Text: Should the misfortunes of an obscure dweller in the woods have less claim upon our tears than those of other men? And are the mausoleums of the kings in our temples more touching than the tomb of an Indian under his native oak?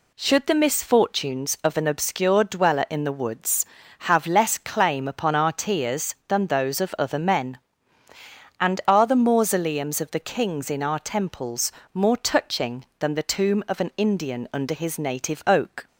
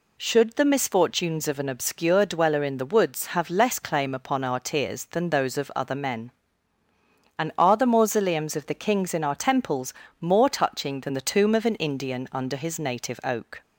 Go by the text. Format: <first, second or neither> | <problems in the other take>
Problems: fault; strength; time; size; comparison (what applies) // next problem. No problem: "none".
neither | pauses between "temples" and "more"; slight; the same in both